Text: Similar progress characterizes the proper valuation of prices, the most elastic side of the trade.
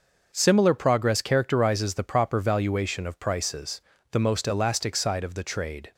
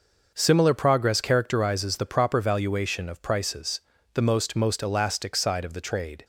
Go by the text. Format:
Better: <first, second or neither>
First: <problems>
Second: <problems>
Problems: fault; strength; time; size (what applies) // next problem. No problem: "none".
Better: first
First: starts louder than the rest; until 1.3 s; 6 dB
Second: starts louder than the rest; noticeable; until 1.3 s; 6 dB // says "most" twice; at 4.5 s